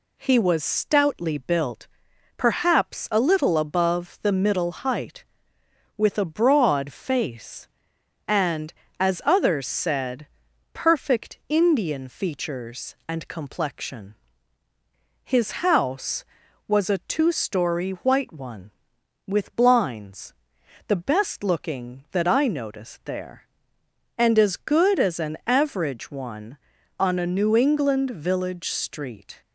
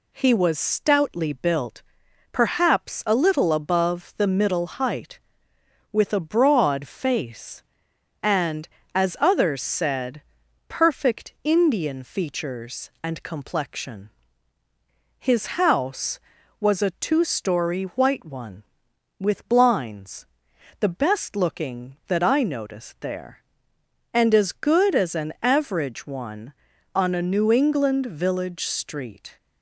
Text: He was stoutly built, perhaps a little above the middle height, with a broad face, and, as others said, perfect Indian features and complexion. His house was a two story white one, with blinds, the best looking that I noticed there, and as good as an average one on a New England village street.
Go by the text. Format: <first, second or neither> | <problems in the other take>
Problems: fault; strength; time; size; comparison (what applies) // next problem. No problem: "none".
neither | none